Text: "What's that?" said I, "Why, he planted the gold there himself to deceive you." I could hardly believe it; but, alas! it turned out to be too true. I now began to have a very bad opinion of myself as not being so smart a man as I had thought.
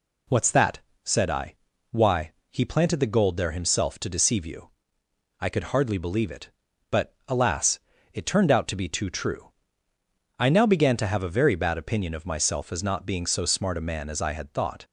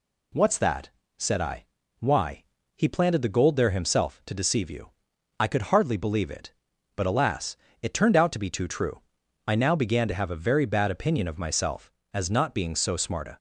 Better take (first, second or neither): first